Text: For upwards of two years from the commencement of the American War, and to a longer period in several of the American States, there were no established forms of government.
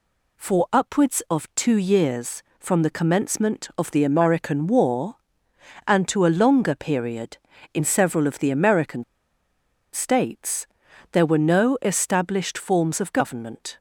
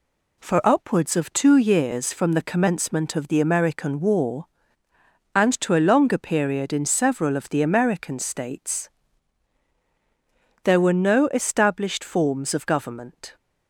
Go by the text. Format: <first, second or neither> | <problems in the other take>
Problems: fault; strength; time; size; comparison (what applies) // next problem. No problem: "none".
second | pauses between "American" and "States"; noticeable; at 9.0 s; 0.90 s long